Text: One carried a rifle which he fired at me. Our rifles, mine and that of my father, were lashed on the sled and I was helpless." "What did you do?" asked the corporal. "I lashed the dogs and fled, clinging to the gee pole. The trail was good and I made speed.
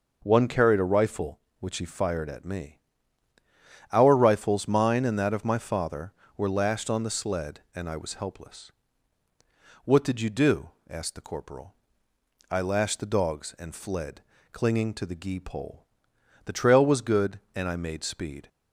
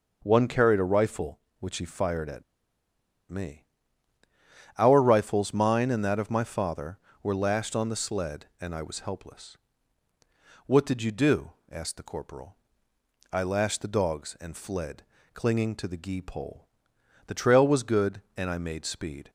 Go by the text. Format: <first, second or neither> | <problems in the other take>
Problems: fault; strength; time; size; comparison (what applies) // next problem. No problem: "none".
first | pauses between "at" and "me"; noticeable; at 2.4 s; 0.86 s long